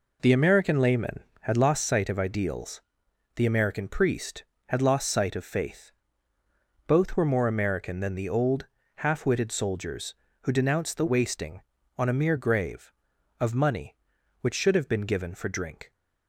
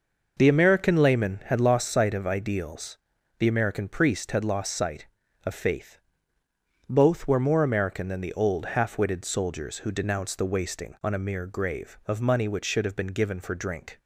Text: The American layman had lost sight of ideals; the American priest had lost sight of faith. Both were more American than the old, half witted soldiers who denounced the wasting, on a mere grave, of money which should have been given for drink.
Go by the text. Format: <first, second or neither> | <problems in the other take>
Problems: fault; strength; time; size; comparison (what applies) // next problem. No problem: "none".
neither | none